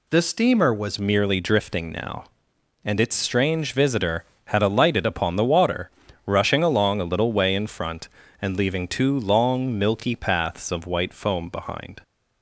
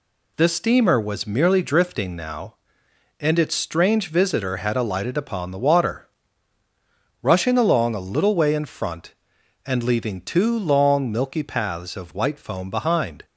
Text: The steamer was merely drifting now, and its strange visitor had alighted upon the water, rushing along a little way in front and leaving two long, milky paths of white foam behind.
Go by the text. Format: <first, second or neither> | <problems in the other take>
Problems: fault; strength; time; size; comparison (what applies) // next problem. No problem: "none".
second | changes voice at "merely"; from 0.9 s on; 11.1 s long